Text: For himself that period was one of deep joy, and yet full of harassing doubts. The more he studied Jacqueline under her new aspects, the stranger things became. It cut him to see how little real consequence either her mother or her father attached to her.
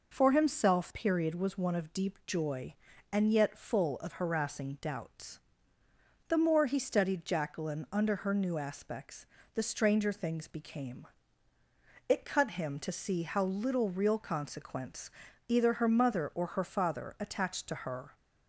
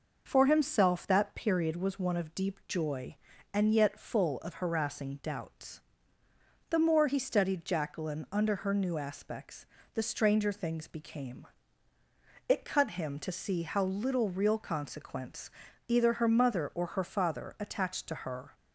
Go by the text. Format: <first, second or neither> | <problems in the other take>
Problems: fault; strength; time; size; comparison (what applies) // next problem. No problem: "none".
second | skips "that"; at 0.9 s // pauses between "consequence" and "either"; slight; at 15.1 s; 0.36 s long; slight in the second